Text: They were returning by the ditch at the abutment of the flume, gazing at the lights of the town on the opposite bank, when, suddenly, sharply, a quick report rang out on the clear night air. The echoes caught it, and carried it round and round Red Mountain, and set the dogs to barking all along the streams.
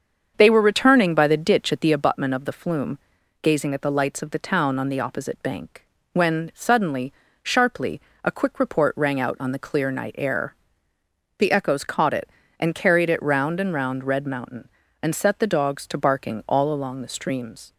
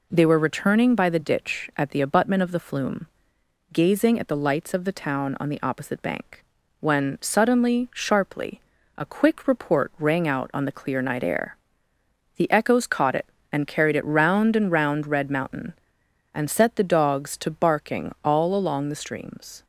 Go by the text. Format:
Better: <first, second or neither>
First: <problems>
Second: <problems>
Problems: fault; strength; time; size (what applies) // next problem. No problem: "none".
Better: second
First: starts louder than the rest; strong; until 2.1 s; 7 dB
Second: none